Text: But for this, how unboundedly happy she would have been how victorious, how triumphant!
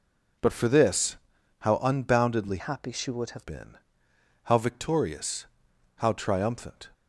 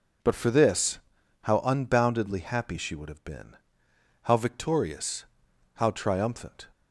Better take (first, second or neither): second